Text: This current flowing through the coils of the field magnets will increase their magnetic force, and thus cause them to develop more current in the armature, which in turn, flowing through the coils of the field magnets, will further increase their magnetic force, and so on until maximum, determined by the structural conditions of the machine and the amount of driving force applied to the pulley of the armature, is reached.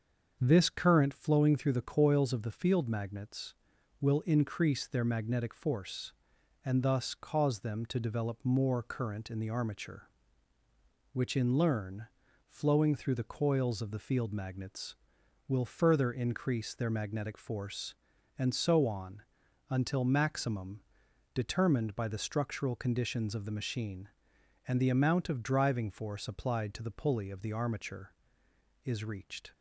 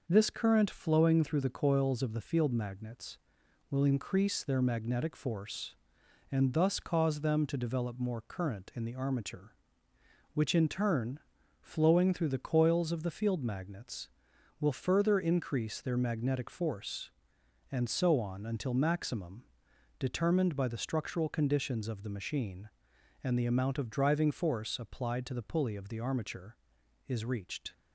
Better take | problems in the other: second | starts louder than the rest; until 1.4 s; 7 dB // says "learn" for "turn"; at 11.5 s // pauses between "on" and "until"; noticeable; at 19.2 s; 0.48 s long

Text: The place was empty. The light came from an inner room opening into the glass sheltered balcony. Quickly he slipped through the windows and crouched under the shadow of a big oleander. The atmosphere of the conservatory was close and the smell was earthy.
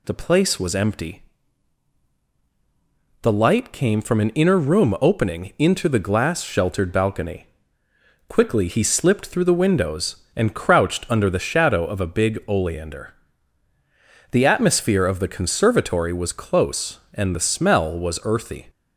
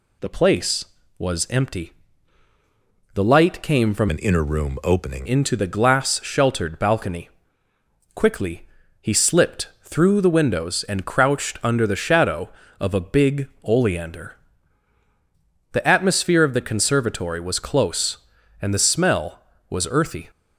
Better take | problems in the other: first | changes voice from "an" to "opening"; from 4.0 to 5.2 s; 1.2 s long // pauses between "Quickly" and "he"; slight; at 8.6 s; 0.34 s long // pauses between "big" and "oleander"; slight; at 13.4 s; 0.16 s long

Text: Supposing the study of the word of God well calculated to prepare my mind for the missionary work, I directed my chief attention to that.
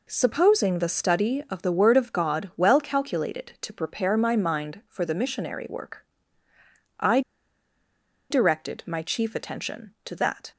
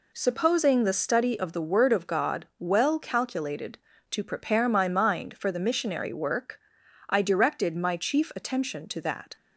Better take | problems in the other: second | pauses between "I" and "directed"; at 7.2 s; 1.1 s long

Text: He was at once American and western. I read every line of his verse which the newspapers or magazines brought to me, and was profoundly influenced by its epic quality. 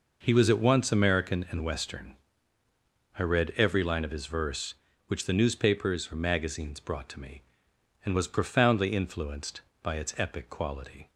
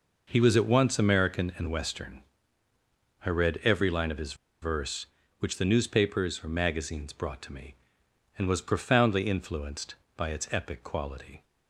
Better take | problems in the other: first | pauses between "his" and "verse"; slight; at 4.3 s; 0.27 s long

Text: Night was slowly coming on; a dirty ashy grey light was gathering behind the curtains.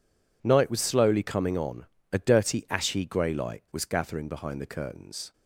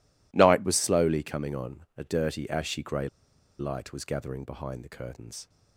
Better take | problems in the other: first | pauses between "grey" and "light"; noticeable; at 3.0 s; 0.52 s long

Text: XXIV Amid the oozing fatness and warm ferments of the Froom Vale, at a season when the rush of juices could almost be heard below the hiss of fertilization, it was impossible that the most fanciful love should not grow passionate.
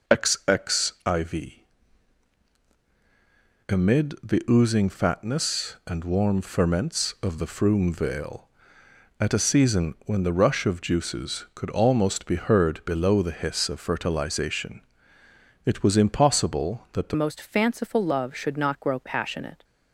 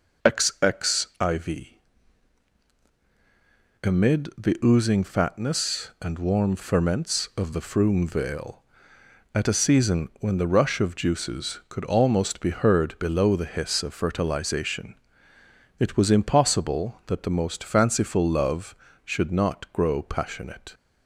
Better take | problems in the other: second | pauses between "XXIV" and "Amid"; strong; at 1.6 s; 2.0 s long; strong in the second // changes voice at "most"; from 17.1 s on; 2.5 s long

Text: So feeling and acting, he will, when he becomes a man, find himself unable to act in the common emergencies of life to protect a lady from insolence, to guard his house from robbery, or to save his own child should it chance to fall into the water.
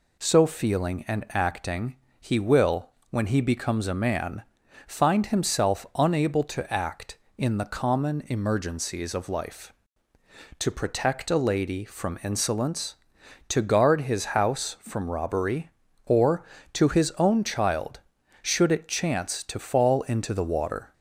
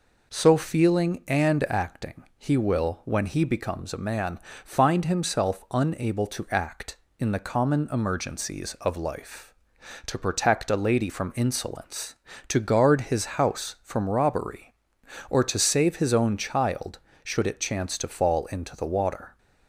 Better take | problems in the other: second | skips "save"; at 16.8 s

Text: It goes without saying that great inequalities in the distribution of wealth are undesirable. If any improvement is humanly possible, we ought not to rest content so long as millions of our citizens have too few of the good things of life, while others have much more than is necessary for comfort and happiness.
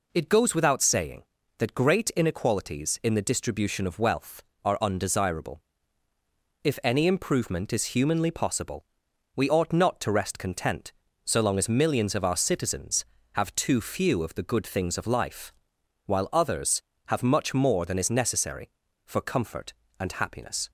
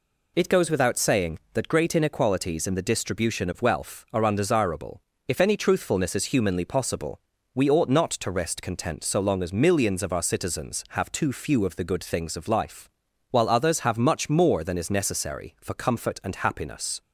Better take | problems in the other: first | says "truthfulness" for "improvement"; at 5.5 s

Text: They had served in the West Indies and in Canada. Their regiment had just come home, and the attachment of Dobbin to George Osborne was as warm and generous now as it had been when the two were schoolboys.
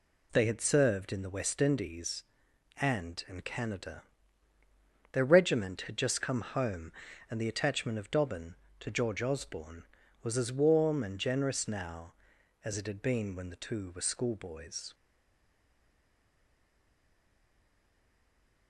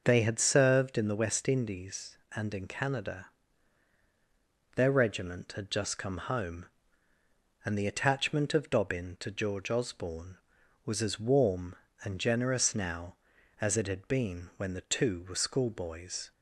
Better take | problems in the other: second | stays silent after the last word; strong; from 14.9 s on; 3.7 s long

